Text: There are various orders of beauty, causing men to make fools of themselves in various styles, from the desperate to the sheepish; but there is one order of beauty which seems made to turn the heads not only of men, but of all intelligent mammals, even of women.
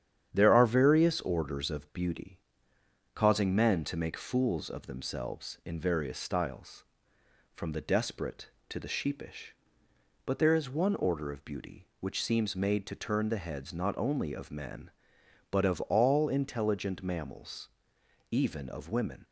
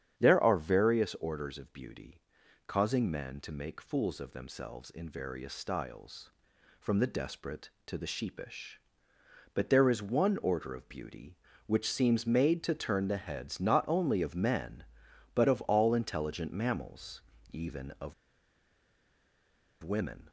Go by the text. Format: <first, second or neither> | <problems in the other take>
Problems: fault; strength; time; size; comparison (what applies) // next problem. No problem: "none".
first | starts louder than the rest; strong; until 1.2 s; 9.5 dB; strong in the first // pauses between "of" and "women"; strong; at 18.1 s; 1.6 s long